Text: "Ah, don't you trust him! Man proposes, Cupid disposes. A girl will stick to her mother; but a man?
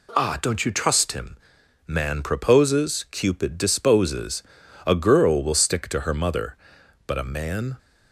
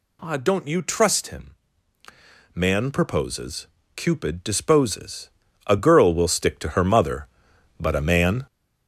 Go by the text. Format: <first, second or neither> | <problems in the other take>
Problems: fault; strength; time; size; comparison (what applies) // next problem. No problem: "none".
first | gets louder; noticeable; throughout; 6 dB